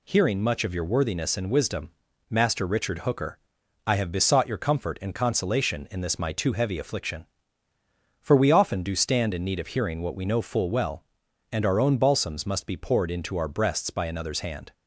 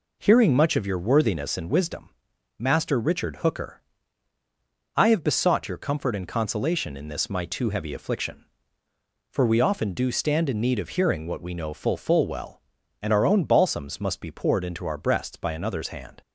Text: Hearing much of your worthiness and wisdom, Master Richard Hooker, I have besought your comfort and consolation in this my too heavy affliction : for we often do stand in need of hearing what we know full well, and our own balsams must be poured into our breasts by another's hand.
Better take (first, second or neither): first